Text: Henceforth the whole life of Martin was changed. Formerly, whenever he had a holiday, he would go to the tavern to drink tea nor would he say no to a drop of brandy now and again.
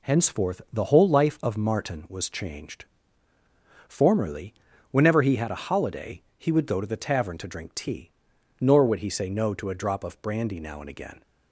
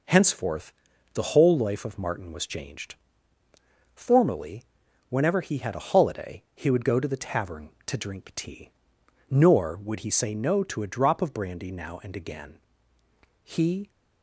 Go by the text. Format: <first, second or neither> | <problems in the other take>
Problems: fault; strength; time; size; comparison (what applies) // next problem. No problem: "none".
first | pauses between "Henceforth" and "the"; at 0.7 s; 0.42 s long // pauses between "tea" and "nor"; noticeable; at 8.6 s; 0.58 s long; noticeable in the first // goes on to say "He"; slight; from 13.4 s on; 0.48 s long